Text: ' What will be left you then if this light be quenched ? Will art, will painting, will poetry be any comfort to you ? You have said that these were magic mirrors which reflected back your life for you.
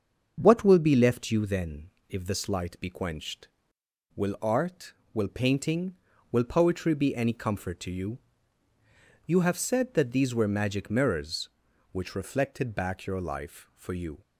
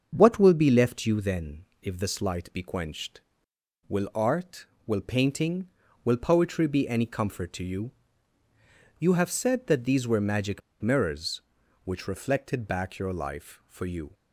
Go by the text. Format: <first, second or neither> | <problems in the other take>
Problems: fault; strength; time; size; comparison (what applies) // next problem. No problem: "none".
first | starts louder than the rest; until 1.1 s; 7 dB; also in the first // pauses between "then" and "if"; slight; at 1.6 s; 0.18 s long; slight in the first // pauses between "magic" and "mirrors"; slight; at 10.6 s; 0.20 s long